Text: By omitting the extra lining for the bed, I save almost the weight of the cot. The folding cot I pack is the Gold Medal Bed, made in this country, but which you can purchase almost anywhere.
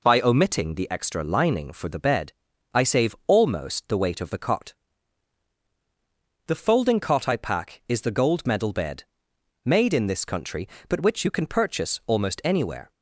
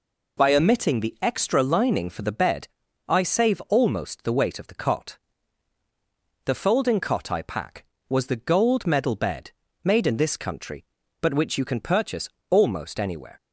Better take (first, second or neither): first